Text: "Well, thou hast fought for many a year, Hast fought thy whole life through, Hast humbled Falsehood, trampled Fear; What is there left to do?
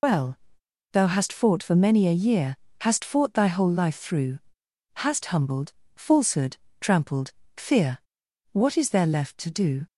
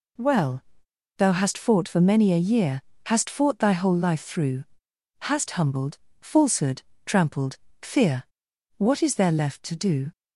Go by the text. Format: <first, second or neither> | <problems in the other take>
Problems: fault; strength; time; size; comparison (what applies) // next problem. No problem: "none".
second | loses the start of "Well"; at 0.0 s; 110 ms // pauses between "humbled" and "Falsehood"; slight; at 5.7 s; 0.24 s long; slight in the second // pauses between "trampled" and "Fear"; slight; at 7.3 s; 0.24 s long; slight in the second